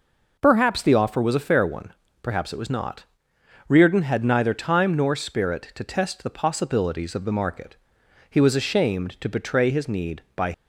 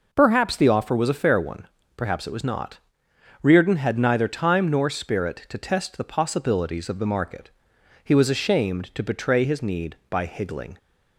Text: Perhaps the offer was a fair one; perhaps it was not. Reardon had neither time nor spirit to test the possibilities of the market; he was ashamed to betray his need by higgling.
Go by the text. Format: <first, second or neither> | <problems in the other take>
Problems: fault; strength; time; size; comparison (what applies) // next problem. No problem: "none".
second | stops before "higgling"; at 10.5 s